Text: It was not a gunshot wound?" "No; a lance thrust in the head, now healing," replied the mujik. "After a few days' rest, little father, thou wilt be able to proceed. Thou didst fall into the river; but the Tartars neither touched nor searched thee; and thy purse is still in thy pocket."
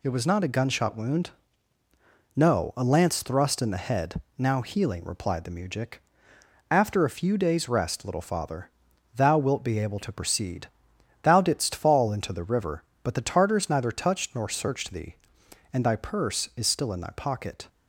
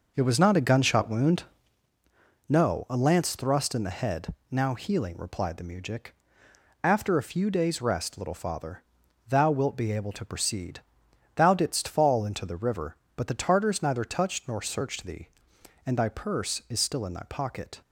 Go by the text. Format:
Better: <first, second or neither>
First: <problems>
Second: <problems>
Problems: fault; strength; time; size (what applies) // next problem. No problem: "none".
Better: first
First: none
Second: starts louder than the rest; noticeable; until 1.9 s; 5.5 dB